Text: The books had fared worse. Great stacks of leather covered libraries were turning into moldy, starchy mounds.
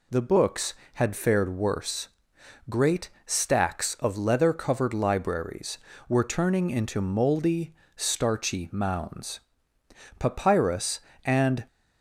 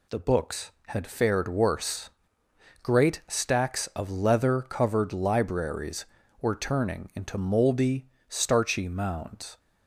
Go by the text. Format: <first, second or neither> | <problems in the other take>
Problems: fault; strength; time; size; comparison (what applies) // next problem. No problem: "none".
second | pauses between "Great" and "stacks"; slight; at 3.0 s; 0.16 s long // goes on to say "Papyrus and"; from 10.1 s on; 1.4 s long